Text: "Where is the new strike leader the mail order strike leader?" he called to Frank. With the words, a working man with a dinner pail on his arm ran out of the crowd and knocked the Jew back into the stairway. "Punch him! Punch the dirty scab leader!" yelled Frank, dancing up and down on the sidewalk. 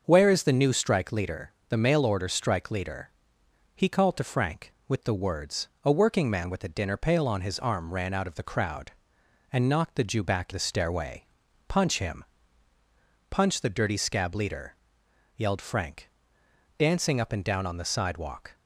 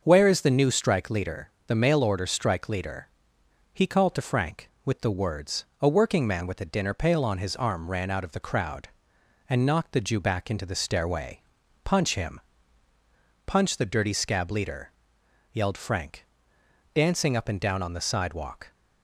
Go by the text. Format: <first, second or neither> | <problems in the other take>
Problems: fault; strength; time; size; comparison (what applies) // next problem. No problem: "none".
second | starts louder than the rest; until 1.0 s; 6.5 dB; also in the second // pauses between "leader" and "the"; slight; at 1.5 s; 0.18 s long; slight in the second // skips "into"; at 10.5 s